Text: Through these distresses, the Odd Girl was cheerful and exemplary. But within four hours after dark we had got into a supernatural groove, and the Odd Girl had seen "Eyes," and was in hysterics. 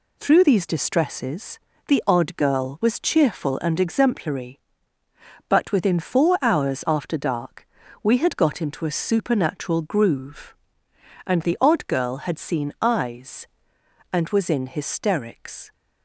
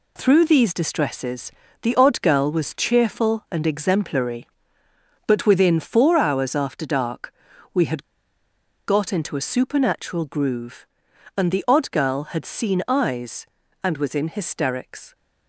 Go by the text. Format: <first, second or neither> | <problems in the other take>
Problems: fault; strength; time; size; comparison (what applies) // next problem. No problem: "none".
first | pauses between "dark" and "we"; at 7.3 s; 0.44 s long; slight in the first // pauses between "had" and "got"; noticeable; at 8.0 s; 0.84 s long